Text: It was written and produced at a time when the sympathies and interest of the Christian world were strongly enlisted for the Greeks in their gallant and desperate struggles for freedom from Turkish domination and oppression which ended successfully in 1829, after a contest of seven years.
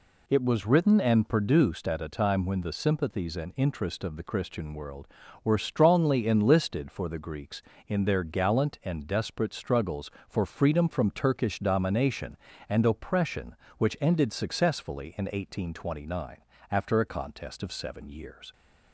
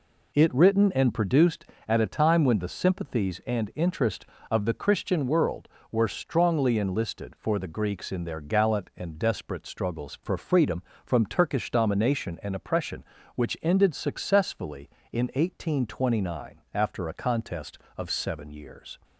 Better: first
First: none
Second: skips "was"; at 0.5 s

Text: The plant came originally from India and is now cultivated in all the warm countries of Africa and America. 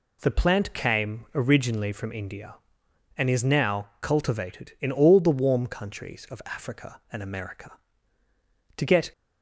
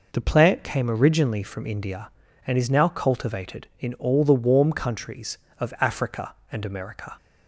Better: second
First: goes on to say "To get"; slight; from 8.7 s on; 0.36 s long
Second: none

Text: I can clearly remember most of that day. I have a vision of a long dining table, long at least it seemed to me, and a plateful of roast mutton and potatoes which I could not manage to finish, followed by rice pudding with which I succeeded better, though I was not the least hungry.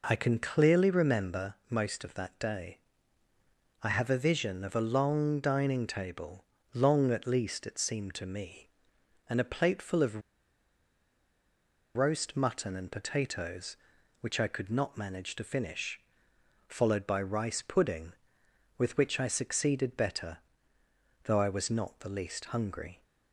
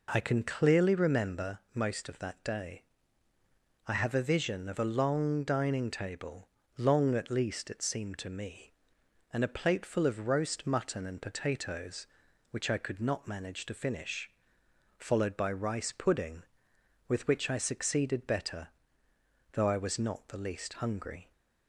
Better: second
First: pauses between "remember" and "most"; slight; at 1.5 s; 0.16 s long // pauses between "of" and "roast"; strong; at 10.2 s; 1.7 s long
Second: pauses between "remember" and "most"; slight; at 1.5 s; 0.16 s long

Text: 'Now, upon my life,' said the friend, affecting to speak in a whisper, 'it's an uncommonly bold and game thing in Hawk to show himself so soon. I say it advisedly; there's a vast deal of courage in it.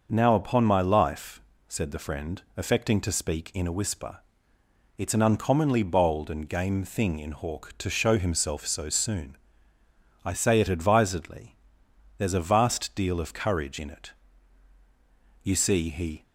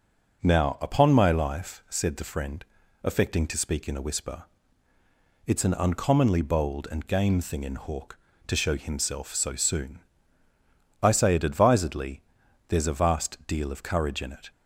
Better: second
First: starts louder than the rest; noticeable; until 1.1 s; 6 dB // goes on to say "You see he"; noticeable; from 15.4 s on; 0.80 s long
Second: none

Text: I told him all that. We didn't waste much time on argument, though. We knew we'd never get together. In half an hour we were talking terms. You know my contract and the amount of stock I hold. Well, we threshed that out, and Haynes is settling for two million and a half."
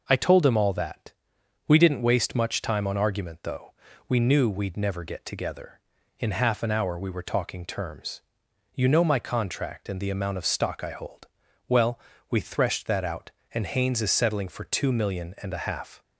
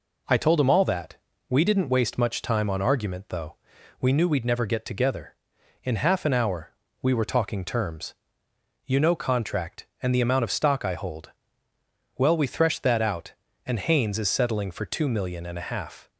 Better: first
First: none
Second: pauses between "hour" and "we"; slight; at 6.6 s; 0.32 s long // skips "my"; at 9.1 s

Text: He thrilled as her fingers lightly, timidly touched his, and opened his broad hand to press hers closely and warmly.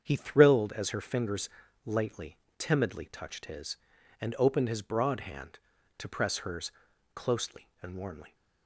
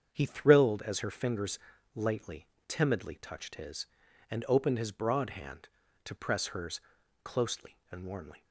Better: neither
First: starts louder than the rest; strong; until 1.0 s; 7.5 dB // pauses between "fingers" and "lightly"; at 1.4 s; 0.38 s long // pauses between "hers" and "closely"; at 6.7 s; 0.44 s long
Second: starts louder than the rest; strong; until 1.1 s; 7.5 dB // pauses between "fingers" and "lightly"; at 1.5 s; 0.38 s long // pauses between "hers" and "closely"; at 6.7 s; 0.44 s long

